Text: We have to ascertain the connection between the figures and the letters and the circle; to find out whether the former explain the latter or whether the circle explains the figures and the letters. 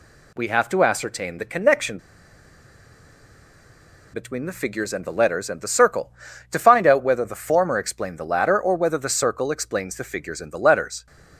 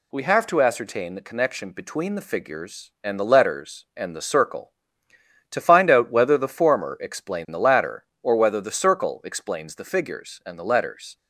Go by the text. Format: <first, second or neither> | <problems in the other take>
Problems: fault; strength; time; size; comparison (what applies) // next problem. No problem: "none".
second | pauses between "connection" and "between"; strong; at 1.9 s; 2.1 s long